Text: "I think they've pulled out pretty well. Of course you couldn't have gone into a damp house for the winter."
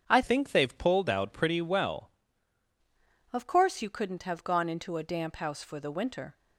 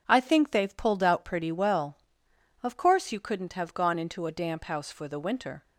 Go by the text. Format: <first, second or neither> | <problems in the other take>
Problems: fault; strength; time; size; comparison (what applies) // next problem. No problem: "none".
second | starts louder than the rest; strong; until 1.0 s; 8 dB // changes voice from "think" to "well"; from 0.2 to 2.1 s; 1.9 s long